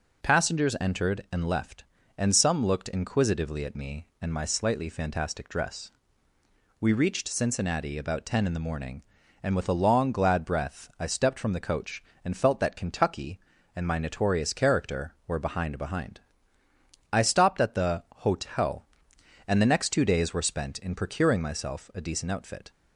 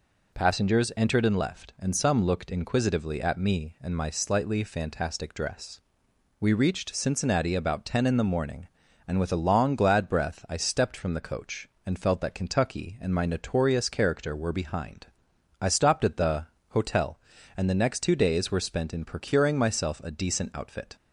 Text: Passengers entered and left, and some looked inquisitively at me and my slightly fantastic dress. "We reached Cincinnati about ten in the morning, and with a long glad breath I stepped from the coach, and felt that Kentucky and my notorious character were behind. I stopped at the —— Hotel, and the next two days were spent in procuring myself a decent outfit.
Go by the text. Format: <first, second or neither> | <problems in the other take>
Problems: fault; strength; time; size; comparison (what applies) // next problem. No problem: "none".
second | says "behind" twice; at 15.7 s